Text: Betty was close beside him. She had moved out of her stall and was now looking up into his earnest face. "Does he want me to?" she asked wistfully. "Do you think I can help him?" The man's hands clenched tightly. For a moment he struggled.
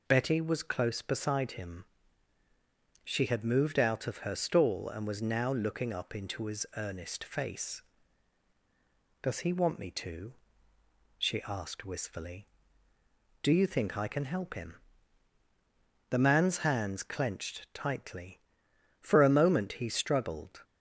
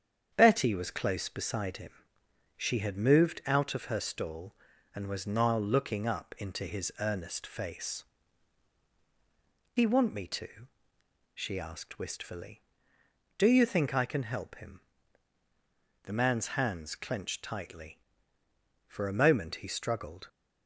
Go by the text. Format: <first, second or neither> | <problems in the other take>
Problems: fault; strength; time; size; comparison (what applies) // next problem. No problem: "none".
first | starts louder than the rest; strong; until 1.3 s; 8 dB // skips "Does"; at 8.9 s